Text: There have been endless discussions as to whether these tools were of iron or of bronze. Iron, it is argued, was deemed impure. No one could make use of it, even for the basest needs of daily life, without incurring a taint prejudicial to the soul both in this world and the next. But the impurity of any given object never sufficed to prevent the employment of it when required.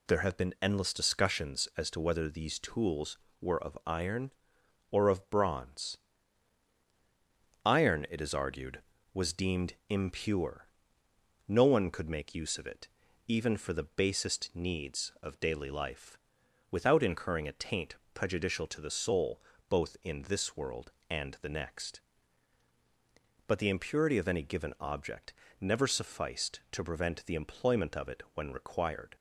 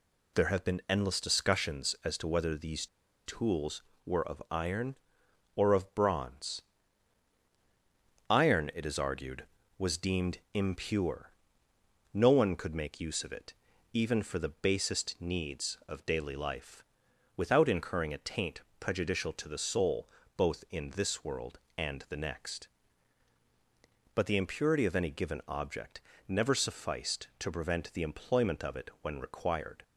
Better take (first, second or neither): first